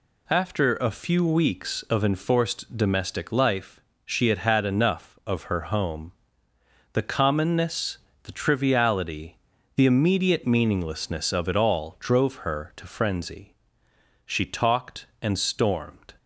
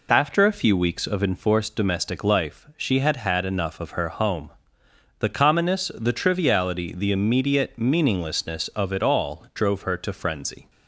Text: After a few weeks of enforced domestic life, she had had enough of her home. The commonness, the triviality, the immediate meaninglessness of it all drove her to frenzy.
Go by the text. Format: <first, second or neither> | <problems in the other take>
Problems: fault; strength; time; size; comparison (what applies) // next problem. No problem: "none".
second | goes on to say "She talked and stormed"; strong; from 14.2 s on; 1.9 s long